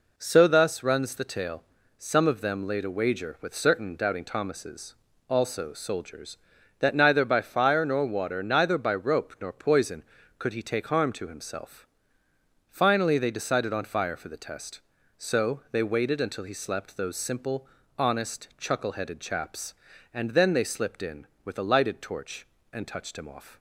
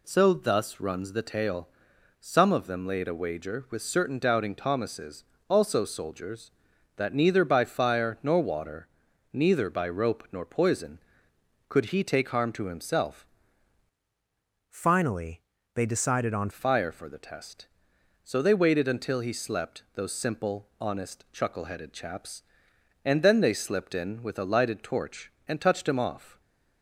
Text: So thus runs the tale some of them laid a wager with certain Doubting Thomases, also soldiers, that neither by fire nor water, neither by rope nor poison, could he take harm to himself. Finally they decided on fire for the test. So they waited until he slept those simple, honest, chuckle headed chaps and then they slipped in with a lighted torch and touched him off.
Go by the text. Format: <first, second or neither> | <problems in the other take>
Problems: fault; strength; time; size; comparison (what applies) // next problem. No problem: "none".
first | pauses between "tale" and "some"; noticeable; at 1.6 s; 0.54 s long; slight in the first // changes voice from "Finally" to "on"; from 14.7 to 16.4 s; 1.7 s long // pauses between "Finally" and "they"; slight; at 15.4 s; 0.32 s long